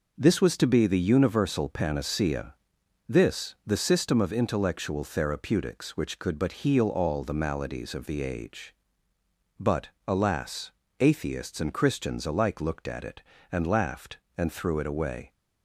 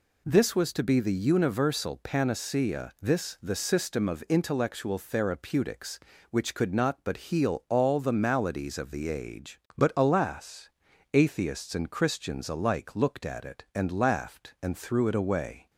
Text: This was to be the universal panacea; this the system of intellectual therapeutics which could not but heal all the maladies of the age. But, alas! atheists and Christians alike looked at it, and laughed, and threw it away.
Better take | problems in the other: second | skips "not"; at 6.3 s

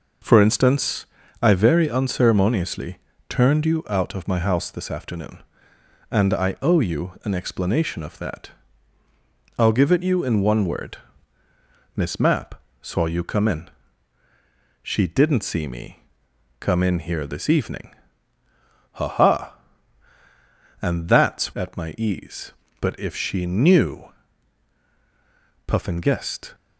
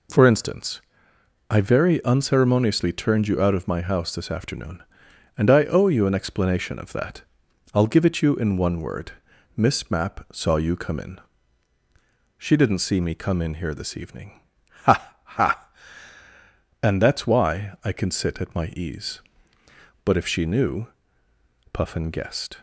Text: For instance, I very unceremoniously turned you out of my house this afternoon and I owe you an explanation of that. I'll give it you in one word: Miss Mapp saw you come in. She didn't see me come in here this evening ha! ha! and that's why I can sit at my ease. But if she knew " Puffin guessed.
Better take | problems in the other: second | pauses between "unceremoniously" and "turned"; slight; at 2.9 s; 0.30 s long // pauses between "Mapp" and "saw"; slight; at 12.5 s; 0.26 s long // pauses between "me" and "come"; noticeable; at 15.9 s; 0.64 s long // pauses between "evening" and "ha"; at 17.9 s; 1.0 s long; also in the second // skips "why I can sit"; at 21.5 s

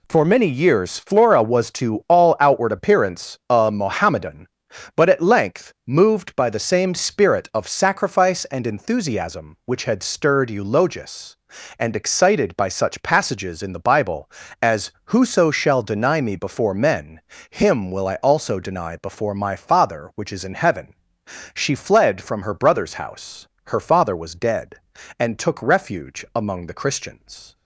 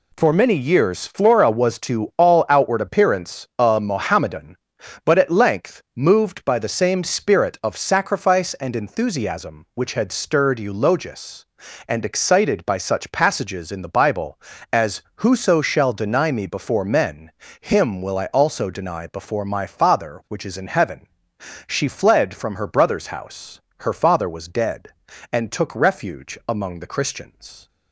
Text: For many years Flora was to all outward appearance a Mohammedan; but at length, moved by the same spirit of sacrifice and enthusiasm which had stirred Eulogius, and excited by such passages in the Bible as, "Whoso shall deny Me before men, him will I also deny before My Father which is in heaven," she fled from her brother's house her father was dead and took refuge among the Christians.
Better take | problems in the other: neither | pauses between "house" and "her"; slight; the same in both

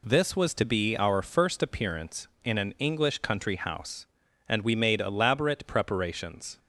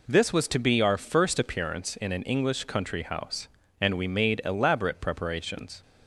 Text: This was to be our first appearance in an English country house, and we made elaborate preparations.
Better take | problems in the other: neither | none

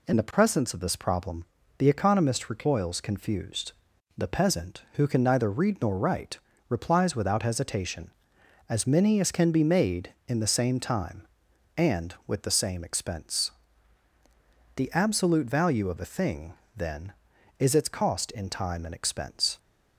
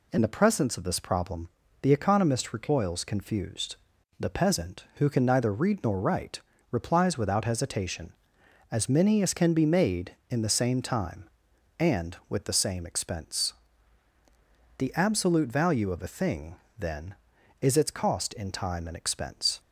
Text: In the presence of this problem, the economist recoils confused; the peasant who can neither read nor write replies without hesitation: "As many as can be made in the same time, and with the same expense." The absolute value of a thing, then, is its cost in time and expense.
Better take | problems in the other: neither | pauses between "write" and "replies"; slight; the same in both

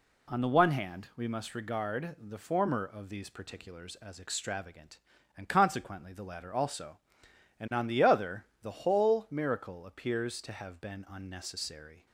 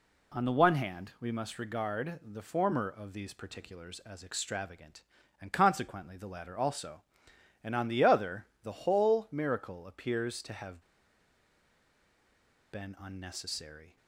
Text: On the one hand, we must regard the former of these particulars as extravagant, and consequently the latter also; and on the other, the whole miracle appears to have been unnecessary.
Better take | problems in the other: first | pauses between "have" and "been"; strong; at 10.8 s; 1.9 s long

